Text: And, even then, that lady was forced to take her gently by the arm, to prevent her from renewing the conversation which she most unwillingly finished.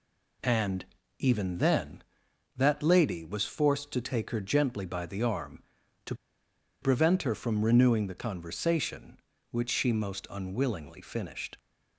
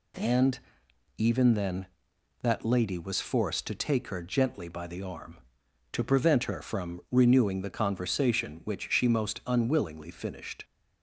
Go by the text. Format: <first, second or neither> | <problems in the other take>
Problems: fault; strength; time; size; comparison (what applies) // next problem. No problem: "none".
second | pauses between "to" and "prevent"; noticeable; at 6.1 s; 0.68 s long